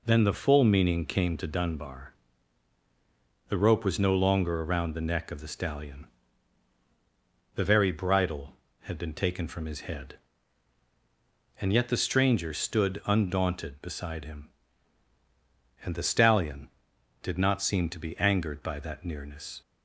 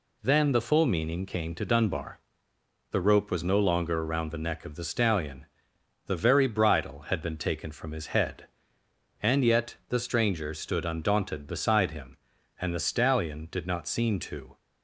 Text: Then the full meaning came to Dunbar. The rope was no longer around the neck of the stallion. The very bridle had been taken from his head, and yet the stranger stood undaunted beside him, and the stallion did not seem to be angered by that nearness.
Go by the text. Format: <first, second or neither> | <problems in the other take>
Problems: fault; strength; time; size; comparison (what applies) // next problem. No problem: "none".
first | stops before "be angered by that nearness"; at 14.5 s